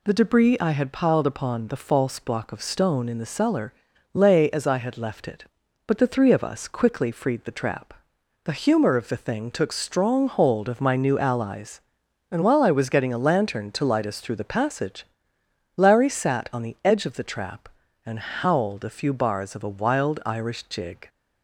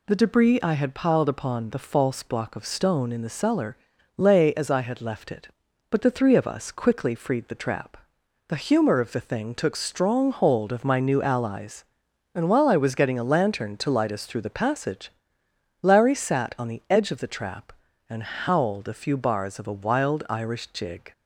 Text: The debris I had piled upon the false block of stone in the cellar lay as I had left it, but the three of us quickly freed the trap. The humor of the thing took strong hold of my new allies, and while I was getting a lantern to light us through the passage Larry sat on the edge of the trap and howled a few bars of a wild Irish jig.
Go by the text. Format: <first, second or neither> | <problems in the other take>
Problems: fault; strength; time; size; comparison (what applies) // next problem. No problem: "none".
neither | pauses between "cellar" and "lay"; the same in both // pauses between "passage" and "Larry"; noticeable; the same in both